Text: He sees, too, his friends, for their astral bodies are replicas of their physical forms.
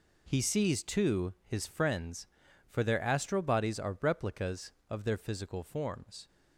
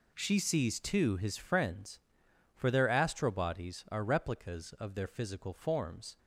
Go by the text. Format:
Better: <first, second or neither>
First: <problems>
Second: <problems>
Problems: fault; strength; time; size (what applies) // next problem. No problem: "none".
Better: first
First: none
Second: says "She" for "He"; at 0.1 s